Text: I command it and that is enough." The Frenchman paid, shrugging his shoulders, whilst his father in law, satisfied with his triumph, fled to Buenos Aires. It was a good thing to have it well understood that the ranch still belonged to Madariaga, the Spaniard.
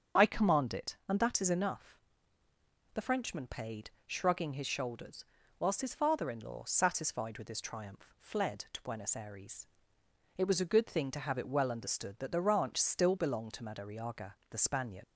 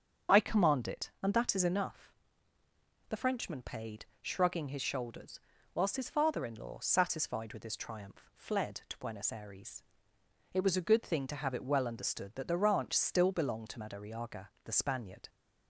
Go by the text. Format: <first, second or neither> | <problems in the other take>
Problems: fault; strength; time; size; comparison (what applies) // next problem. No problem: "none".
second | starts louder than the rest; strong; until 1.2 s; 7.5 dB; strong in the second // leaves "Spaniard" unfinished; at 15.0 s; 105 ms